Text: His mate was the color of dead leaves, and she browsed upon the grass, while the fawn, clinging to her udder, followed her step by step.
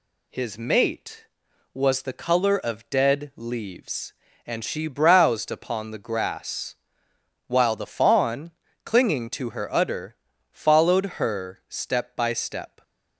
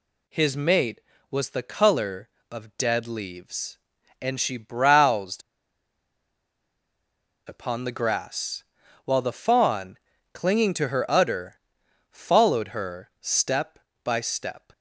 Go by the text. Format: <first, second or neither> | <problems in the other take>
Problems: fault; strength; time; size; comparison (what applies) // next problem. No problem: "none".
first | pauses between "browsed" and "upon"; strong; at 5.4 s; 2.0 s long